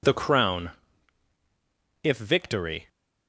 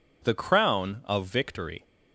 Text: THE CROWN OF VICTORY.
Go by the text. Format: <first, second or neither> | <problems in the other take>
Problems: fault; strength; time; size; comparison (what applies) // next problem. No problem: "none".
second | says "If" for "OF"; at 2.0 s